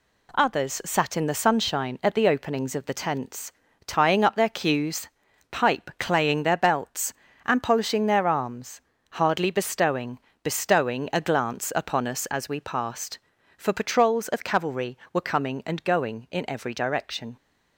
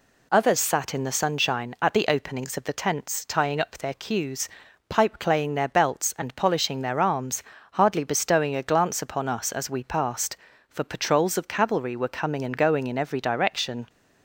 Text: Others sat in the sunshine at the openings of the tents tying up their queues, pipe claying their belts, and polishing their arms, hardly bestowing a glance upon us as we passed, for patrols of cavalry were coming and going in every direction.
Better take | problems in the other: second | pauses between "tents" and "tying"; slight; at 3.5 s; 0.34 s long // says "bestowing" twice; at 10.4 s

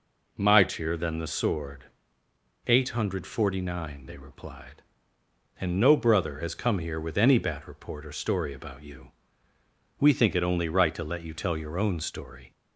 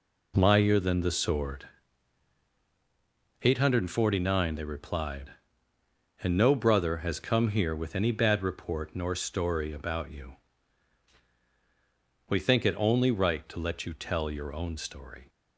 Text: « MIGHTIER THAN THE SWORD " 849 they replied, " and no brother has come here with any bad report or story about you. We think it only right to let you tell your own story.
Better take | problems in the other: first | says "nor" for "or"; at 8.9 s

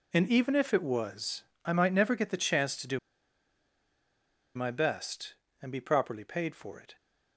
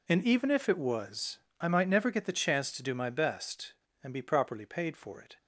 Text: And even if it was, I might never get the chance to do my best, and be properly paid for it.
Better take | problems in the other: second | pauses between "do" and "my"; strong; at 2.9 s; 1.5 s long

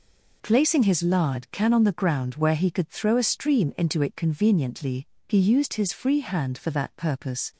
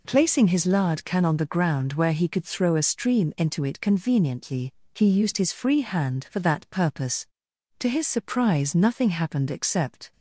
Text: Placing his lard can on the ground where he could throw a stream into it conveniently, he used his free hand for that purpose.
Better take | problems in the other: first | goes on to say "To his surprise nothing happened except"; strong; from 7.7 s on; 2.3 s long

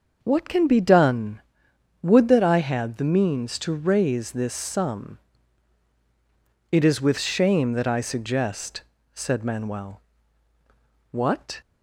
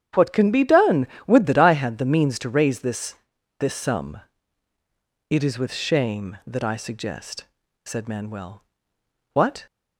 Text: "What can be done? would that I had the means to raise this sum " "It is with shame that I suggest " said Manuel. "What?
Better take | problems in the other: first | starts louder than the rest; strong; until 1.3 s; 9.5 dB; also in the first // says "this" twice; at 3.5 s

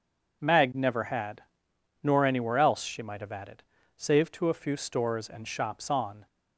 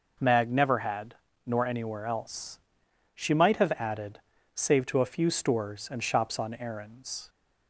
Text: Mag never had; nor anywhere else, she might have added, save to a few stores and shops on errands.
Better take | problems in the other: second | stops before "errands"; at 6.2 s

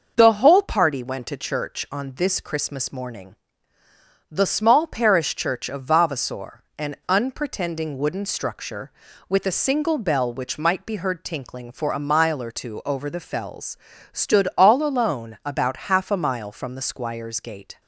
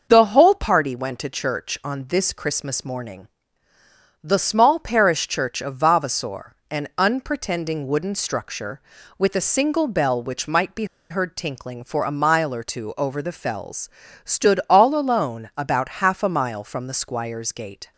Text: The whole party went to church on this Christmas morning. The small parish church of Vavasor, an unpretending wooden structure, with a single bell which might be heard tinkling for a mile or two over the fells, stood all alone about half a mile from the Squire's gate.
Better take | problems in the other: first | starts louder than the rest; noticeable; until 1.1 s; 6 dB; noticeable in the first // pauses between "be" and "heard"; slight; at 10.8 s; 0.24 s long

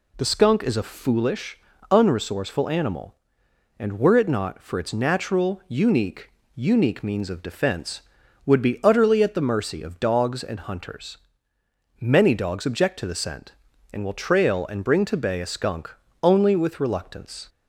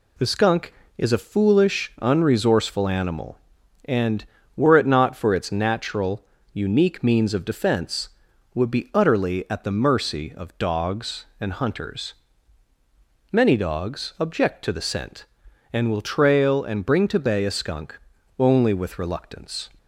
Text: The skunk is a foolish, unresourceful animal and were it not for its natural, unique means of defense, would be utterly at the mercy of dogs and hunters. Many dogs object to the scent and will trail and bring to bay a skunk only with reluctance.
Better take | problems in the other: second | says "unique" twice; at 6.5 s // pauses between "skunk" and "only"; slight; at 15.9 s; 0.30 s long; also in the second

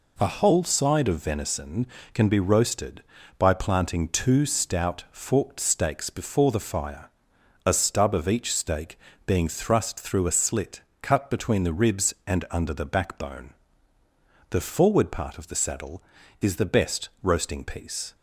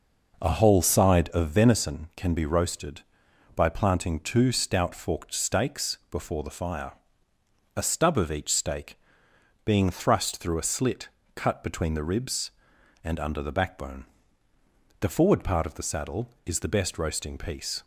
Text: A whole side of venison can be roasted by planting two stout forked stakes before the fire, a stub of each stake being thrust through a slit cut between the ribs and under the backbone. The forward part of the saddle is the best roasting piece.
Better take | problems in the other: first | starts louder than the rest; noticeable; until 1.8 s; 5.5 dB // pauses between "stake" and "being"; noticeable; at 8.9 s; 0.66 s long; slight in the first // pauses between "slit" and "cut"; slight; at 11.0 s; 0.26 s long; slight in the first

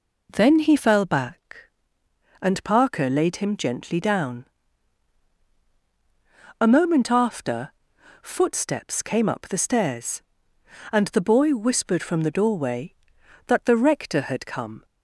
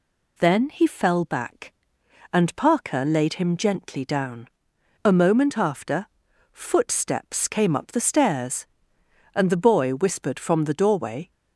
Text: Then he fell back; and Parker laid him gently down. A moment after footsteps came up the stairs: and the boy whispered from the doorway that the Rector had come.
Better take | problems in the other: first | pauses between "after" and "footsteps"; noticeable; at 6.0 s; 0.46 s long; noticeable in the first // stops before "that the Rector had come"; at 11.3 s

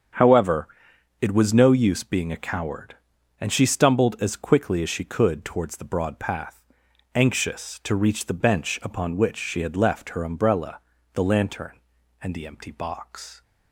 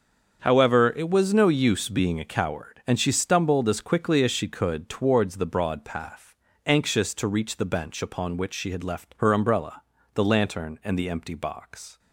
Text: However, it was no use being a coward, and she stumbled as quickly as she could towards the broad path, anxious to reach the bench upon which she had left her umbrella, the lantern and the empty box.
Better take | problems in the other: neither | starts louder than the rest; the same in both

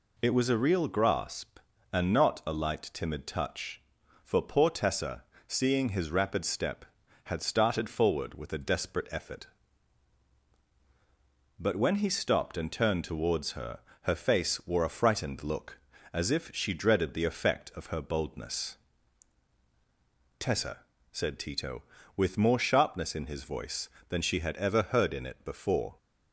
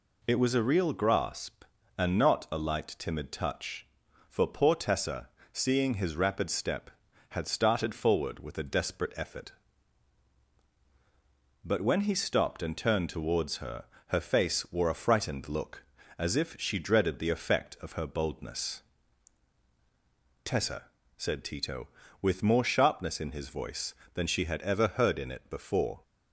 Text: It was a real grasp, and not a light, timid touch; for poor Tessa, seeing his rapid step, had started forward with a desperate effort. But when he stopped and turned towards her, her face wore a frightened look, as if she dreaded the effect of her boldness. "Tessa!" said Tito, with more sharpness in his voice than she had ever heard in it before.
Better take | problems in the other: neither | none

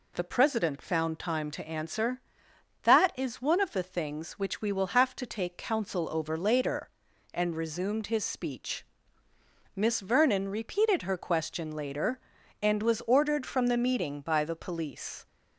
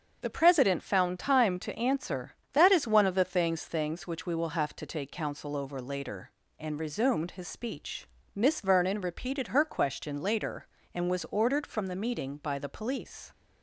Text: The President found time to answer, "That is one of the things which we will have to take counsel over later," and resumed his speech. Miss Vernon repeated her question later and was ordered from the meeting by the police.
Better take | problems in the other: first | starts louder than the rest; until 1.2 s; 7 dB // says "things" twice; at 3.6 s

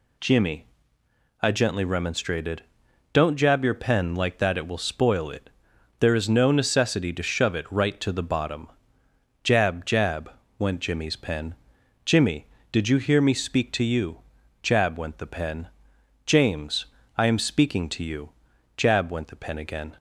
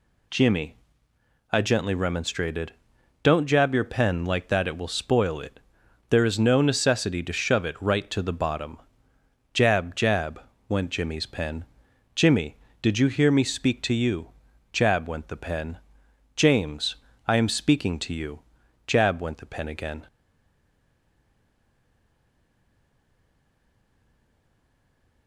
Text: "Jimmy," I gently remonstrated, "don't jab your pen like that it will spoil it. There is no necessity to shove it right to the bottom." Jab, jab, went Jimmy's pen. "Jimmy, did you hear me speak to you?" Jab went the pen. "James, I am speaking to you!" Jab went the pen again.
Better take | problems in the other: first | stays silent after the last word; strong; from 20.0 s on; 5.2 s long

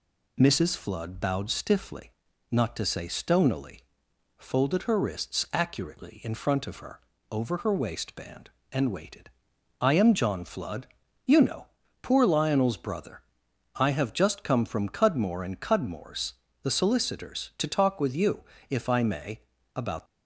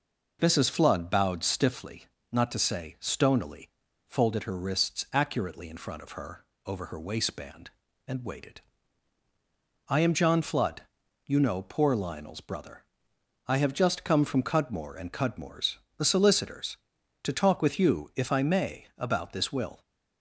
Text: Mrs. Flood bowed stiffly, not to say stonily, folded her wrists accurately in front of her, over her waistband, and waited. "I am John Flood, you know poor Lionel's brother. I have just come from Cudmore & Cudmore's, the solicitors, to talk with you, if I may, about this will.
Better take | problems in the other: second | pauses between "know" and "poor"; slight; at 11.6 s; 0.36 s long // stops before "this will"; at 20.0 s

